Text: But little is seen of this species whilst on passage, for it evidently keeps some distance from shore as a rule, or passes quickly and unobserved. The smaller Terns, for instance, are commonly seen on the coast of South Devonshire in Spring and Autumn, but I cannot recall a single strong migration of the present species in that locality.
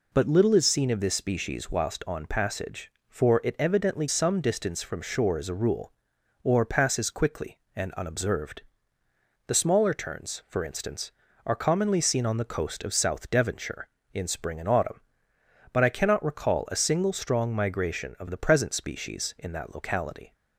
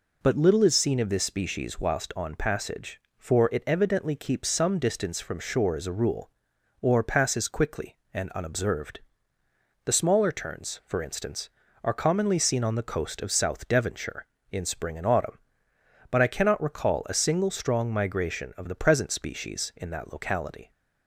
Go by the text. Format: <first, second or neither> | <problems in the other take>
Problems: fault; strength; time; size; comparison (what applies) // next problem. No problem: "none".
second | skips "keeps"; at 4.0 s